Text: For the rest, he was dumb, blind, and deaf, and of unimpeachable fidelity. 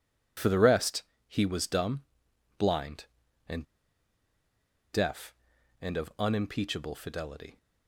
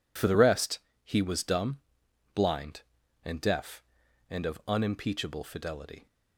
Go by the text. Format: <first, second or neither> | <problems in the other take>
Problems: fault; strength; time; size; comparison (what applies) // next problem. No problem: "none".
second | pauses between "and" and "deaf"; strong; at 3.6 s; 1.2 s long